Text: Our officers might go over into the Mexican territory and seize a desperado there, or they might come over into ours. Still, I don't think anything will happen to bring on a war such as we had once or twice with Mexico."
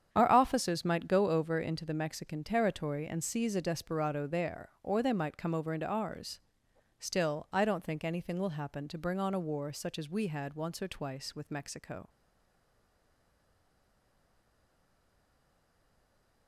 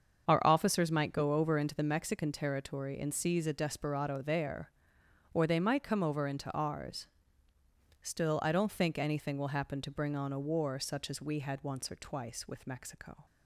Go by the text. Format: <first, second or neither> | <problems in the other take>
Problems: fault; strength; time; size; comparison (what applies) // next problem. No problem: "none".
second | starts louder than the rest; strong; until 1.1 s; 8.5 dB; also in the second // stays silent after the last word; strong; from 12.0 s on; 4.4 s long